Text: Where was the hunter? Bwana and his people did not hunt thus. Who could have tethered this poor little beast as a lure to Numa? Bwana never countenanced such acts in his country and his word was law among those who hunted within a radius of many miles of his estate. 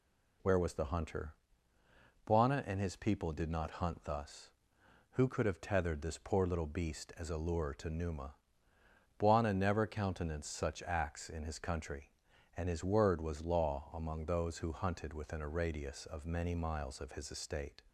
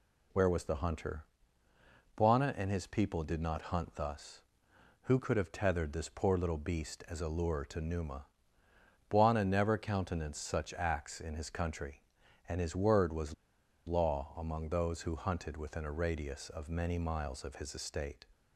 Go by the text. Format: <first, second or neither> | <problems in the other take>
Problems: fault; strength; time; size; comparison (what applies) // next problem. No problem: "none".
first | pauses between "was" and "law"; noticeable; at 13.3 s; 0.53 s long